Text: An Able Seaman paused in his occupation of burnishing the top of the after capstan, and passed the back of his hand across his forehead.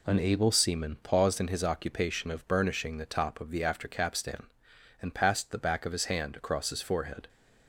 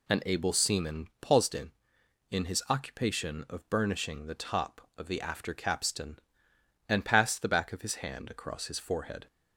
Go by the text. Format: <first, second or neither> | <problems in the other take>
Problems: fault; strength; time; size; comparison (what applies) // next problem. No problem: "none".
first | says "in" twice; at 2.3 s